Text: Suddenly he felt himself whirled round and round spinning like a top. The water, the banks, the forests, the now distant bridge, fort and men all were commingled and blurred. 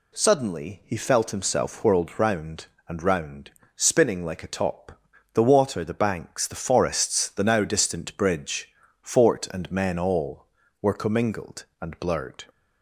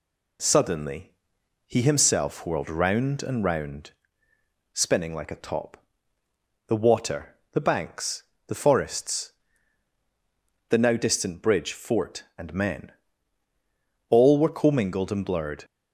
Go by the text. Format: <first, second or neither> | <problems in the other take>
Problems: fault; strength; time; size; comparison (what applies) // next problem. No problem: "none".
first | pauses between "Suddenly" and "he"; noticeable; at 1.1 s; 0.54 s long // skips "felt"; at 1.8 s // pauses between "round" and "spinning"; noticeable; at 3.9 s; 0.82 s long; slight in the first // pauses between "men" and "all"; at 12.9 s; 1.1 s long